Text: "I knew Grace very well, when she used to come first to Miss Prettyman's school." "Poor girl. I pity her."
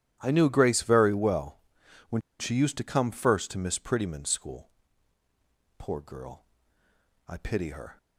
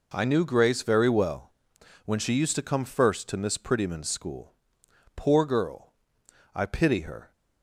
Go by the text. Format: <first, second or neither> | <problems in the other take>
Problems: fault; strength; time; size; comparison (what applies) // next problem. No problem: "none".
second | starts louder than the rest; strong; until 1.2 s; 11.5 dB // pauses between "when" and "she"; slight; at 2.2 s; 0.18 s long